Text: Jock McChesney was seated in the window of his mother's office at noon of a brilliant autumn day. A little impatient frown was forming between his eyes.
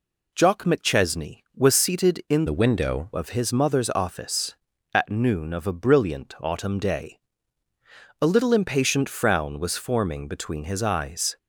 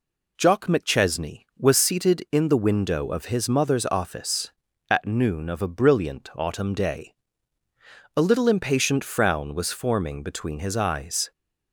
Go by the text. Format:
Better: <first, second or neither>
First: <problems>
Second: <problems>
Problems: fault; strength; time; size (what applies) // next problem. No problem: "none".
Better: second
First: changes voice from "the" to "window"; from 2.4 to 3.1 s; 0.7 s long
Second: none